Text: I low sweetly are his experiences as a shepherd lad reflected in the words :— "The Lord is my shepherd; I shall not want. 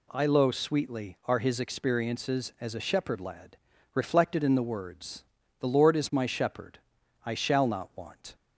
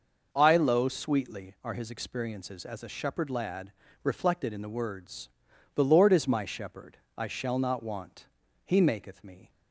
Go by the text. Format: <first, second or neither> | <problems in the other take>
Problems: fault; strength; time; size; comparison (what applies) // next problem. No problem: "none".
first | pauses between "lad" and "reflected"; slight; at 3.7 s; 0.32 s long; slight in the first // goes on to say "He maketh me"; noticeable; from 8.6 s on; 0.86 s long